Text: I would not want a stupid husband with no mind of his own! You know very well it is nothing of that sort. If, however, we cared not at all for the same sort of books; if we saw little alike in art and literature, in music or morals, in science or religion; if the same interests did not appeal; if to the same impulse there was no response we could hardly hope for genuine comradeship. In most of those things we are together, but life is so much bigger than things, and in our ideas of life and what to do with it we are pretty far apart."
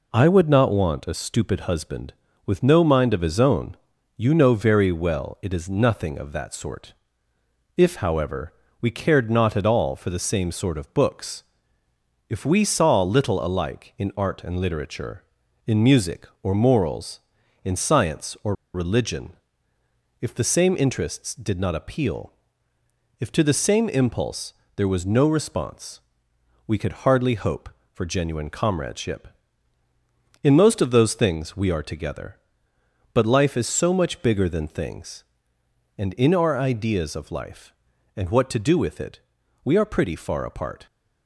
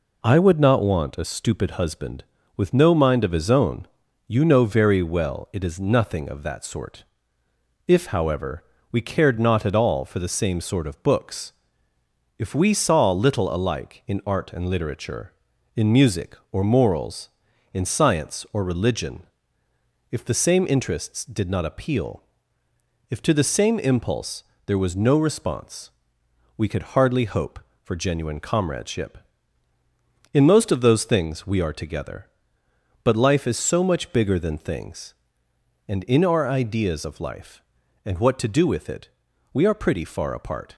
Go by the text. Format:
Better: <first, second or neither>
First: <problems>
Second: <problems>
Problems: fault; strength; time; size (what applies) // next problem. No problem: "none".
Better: second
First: pauses between "or" and "religion"; slight; at 18.5 s; 0.19 s long // pauses between "impulse" and "there"; slight; at 24.5 s; 0.20 s long // pauses between "response" and "we"; noticeable; at 25.9 s; 0.66 s long // pauses between "it" and "we"; at 39.1 s; 0.44 s long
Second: pauses between "impulse" and "there"; slight; at 24.4 s; 0.20 s long // pauses between "response" and "we"; noticeable; at 25.9 s; 0.66 s long // pauses between "it" and "we"; at 39.0 s; 0.44 s long